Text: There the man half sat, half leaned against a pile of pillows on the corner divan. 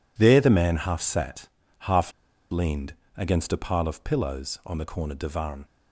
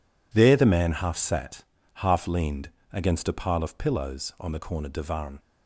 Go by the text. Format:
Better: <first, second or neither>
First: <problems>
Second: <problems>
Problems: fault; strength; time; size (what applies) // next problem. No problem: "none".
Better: second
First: pauses between "half" and "leaned"; at 2.0 s; 0.41 s long // pauses between "leaned" and "against"; slight; at 2.9 s; 0.24 s long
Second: pauses between "leaned" and "against"; slight; at 2.6 s; 0.24 s long